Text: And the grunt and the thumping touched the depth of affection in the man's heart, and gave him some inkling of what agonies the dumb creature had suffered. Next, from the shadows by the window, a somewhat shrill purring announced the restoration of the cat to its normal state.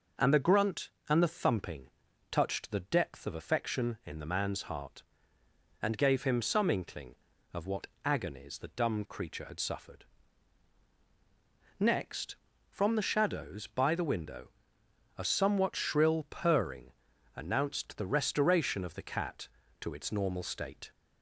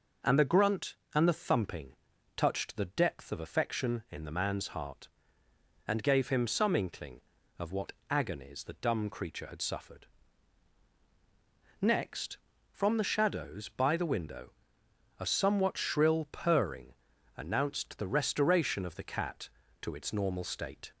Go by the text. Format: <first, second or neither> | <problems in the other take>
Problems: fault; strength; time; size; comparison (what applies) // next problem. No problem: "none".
neither | pauses between "thumping" and "touched"; the same in both // pauses between "what" and "agonies"; slight; the same in both // pauses between "purring" and "announced"; the same in both